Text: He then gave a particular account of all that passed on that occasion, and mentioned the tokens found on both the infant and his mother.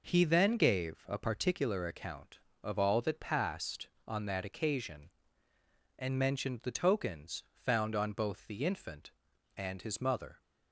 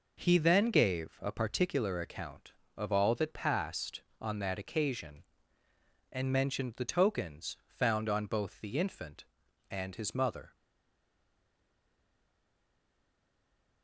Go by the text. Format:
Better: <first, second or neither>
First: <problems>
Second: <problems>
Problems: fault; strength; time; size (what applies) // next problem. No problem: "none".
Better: first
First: none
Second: stays silent after the last word; strong; from 10.5 s on; 3.3 s long